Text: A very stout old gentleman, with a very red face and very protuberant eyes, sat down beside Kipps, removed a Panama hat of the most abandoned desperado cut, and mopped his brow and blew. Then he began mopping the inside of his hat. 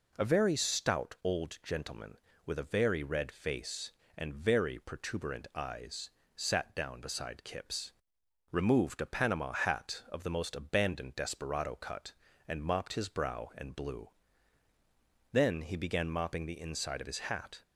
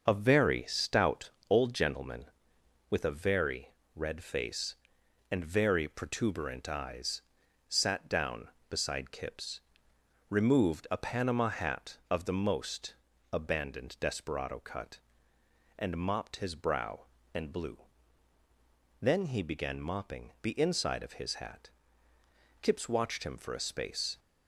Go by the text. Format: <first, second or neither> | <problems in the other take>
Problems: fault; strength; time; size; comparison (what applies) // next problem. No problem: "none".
first | starts louder than the rest; noticeable; until 1.1 s; 6 dB // pauses between "stout" and "old"; slight; at 1.3 s; 0.20 s long // pauses between "very" and "red"; slight; at 3.7 s; 0.22 s long // pauses between "most" and "abandoned"; at 12.9 s; 0.40 s long // goes on to say "Kipps watched him for a space"; from 22.6 s on; 1.5 s long